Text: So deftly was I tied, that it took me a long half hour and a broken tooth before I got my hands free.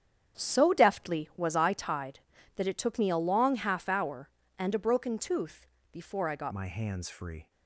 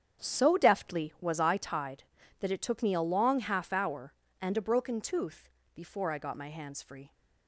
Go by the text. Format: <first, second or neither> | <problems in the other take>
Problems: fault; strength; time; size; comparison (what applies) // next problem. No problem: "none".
second | starts louder than the rest; strong; until 1.4 s; 8.5 dB; strong in the second // pauses between "tooth" and "before"; slight; at 5.6 s; 0.26 s long; slight in the second // changes voice at "my"; from 6.5 s on; 0.9 s long